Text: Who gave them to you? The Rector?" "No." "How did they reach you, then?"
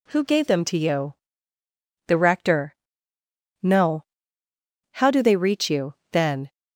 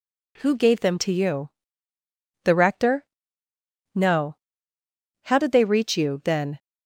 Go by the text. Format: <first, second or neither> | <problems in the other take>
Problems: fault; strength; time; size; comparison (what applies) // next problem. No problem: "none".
second | says "do" for "did"; at 5.0 s